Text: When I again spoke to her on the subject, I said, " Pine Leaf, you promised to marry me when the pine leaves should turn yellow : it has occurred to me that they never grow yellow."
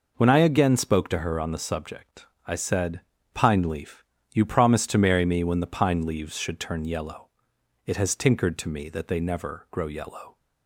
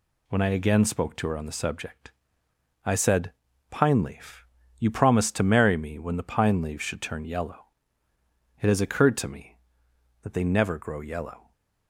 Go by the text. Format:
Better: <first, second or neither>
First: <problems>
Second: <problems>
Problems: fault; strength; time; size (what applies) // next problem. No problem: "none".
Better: second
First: says "tinkered" for "occurred"; at 8.1 s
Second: none